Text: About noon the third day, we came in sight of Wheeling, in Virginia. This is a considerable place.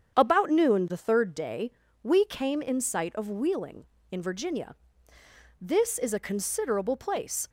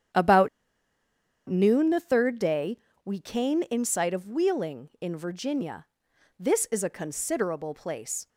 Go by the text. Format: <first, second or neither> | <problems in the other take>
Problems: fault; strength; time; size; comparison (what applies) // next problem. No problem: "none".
first | starts louder than the rest; strong; until 2.1 s; 9.5 dB; strong in the first // pauses between "About" and "noon"; at 0.4 s; 0.99 s long